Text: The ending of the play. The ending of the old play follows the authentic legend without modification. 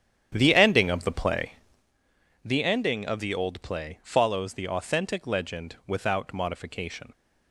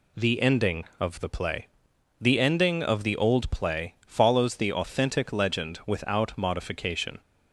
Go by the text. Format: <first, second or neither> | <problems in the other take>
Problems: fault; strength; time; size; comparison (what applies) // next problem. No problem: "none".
second | starts louder than the rest; strong; until 1.9 s; 9.5 dB